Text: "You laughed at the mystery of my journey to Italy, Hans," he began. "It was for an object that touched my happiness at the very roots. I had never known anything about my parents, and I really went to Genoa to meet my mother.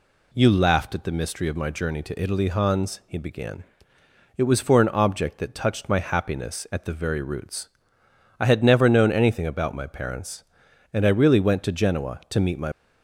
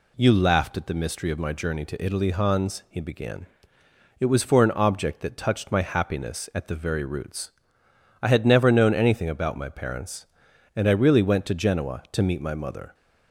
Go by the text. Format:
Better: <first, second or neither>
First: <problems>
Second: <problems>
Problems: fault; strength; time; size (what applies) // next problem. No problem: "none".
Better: second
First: stops before "mother"; at 12.7 s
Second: none